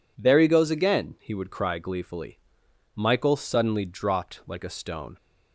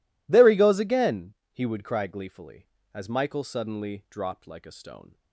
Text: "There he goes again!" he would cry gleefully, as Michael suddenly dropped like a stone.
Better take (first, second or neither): second